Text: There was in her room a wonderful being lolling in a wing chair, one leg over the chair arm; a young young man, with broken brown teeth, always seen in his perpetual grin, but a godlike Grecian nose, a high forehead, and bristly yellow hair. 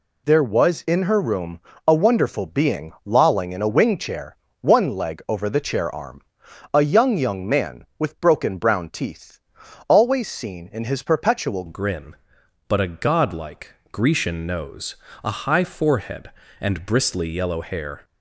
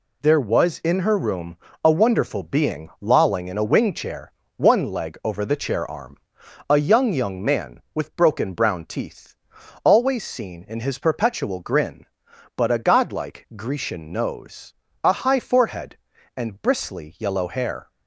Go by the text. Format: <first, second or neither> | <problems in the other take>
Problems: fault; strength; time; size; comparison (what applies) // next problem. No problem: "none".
second | pauses between "room" and "a"; slight; at 1.6 s; 0.26 s long; slight in the second // changes voice at "grin"; from 11.6 s on; 6.4 s long // pauses between "godlike" and "Grecian"; slight; at 13.7 s; 0.20 s long